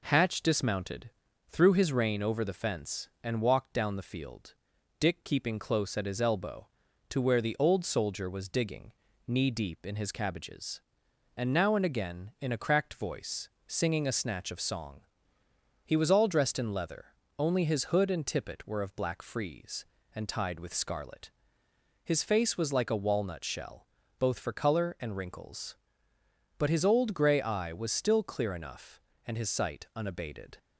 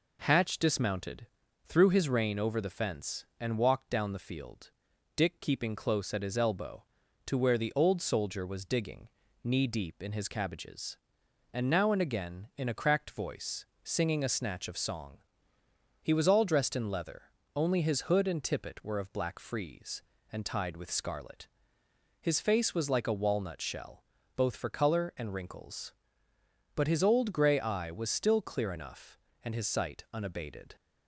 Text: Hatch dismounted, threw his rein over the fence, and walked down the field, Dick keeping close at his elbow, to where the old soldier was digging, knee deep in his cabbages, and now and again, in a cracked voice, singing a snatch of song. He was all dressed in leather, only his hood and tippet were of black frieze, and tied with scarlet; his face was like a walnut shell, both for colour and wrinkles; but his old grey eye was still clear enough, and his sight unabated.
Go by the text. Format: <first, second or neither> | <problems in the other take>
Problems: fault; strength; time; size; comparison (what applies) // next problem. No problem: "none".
neither | none